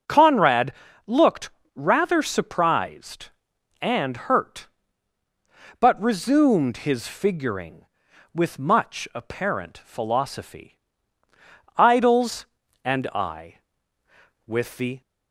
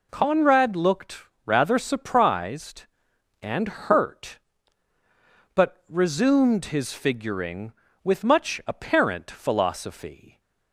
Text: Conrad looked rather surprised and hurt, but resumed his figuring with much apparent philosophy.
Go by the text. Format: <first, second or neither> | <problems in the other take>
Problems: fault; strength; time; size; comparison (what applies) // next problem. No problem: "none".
second | starts louder than the rest; until 1.4 s; 6 dB // pauses between "Conrad" and "looked"; slight; at 0.7 s; 0.34 s long // pauses between "looked" and "rather"; slight; at 1.4 s; 0.26 s long; slight in the second // goes on to say "Idols and I with the"; strong; from 11.7 s on; 3.2 s long